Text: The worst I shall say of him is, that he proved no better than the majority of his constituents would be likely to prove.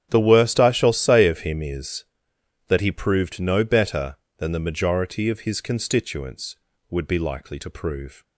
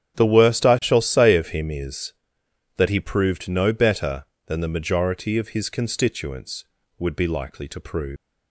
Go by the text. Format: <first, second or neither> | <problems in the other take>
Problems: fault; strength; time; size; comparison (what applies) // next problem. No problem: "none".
first | starts louder than the rest; strong; until 1.2 s; 10 dB; strong in the first // leaves "prove" unfinished; at 8.1 s; 170 ms